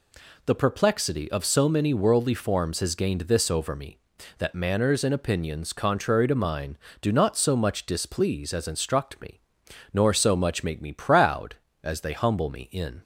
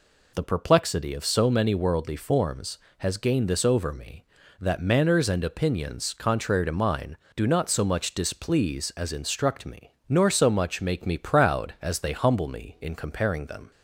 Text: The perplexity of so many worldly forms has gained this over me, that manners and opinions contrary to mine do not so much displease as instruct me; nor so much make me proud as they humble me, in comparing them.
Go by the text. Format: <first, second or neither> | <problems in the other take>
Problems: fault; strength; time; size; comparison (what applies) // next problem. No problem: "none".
second | stops before "comparing them"; at 13.0 s